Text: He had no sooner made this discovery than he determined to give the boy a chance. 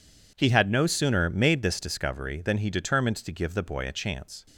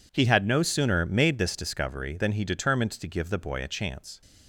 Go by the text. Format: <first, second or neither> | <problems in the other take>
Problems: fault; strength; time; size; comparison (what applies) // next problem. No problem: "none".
neither | none